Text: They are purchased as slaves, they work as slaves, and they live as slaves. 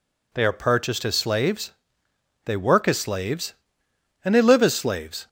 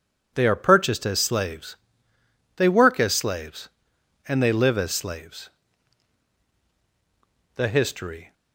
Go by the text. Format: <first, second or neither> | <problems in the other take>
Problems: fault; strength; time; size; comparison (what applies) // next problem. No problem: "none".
first | goes on to say "The history"; noticeable; from 7.5 s on; 0.78 s long